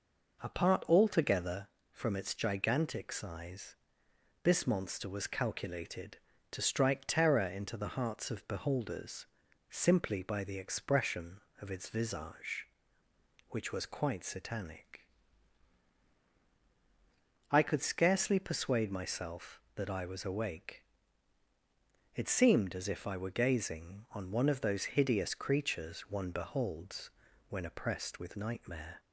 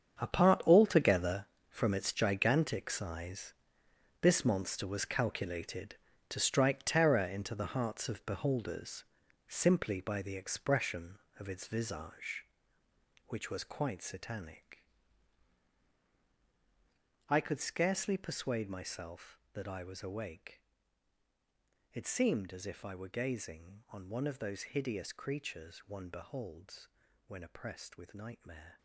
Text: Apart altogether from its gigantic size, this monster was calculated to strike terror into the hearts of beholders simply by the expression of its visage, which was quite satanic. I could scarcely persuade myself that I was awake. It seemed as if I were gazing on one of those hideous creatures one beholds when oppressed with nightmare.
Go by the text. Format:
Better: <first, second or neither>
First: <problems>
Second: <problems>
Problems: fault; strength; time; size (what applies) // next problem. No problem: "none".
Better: first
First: pauses between "beholders" and "simply"; at 9.2 s; 0.44 s long // pauses between "beholds" and "when"; at 27.0 s; 0.38 s long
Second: gets quieter; strong; throughout; 13.5 dB // pauses between "beholders" and "simply"; at 9.0 s; 0.44 s long // pauses between "beholds" and "when"; at 26.8 s; 0.38 s long